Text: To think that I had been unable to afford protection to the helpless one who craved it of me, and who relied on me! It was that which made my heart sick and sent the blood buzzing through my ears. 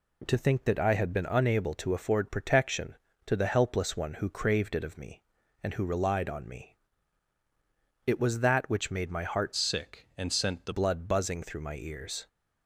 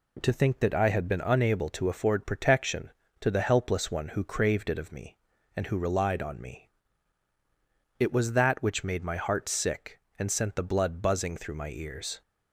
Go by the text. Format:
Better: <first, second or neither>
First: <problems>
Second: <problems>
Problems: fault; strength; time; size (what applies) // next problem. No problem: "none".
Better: second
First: changes voice from "sick" to "the"; from 9.5 to 10.7 s; 1.2 s long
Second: none